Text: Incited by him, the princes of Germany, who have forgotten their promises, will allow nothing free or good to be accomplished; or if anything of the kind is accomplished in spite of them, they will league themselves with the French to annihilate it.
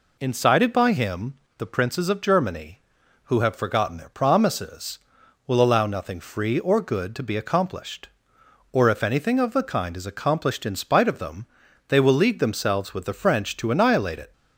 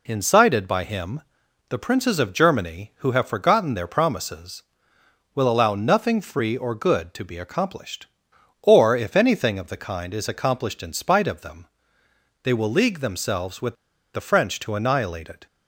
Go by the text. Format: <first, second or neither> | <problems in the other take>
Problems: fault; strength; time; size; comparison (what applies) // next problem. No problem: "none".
first | pauses between "with" and "the"; at 13.7 s; 0.40 s long